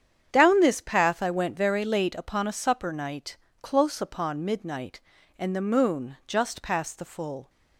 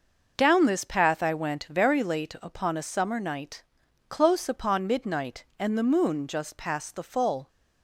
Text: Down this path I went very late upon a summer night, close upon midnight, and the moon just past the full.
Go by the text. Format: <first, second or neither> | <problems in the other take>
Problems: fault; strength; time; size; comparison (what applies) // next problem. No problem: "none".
second | starts louder than the rest; strong; until 1.3 s; 8.5 dB // says "supper" for "summer"; at 2.5 s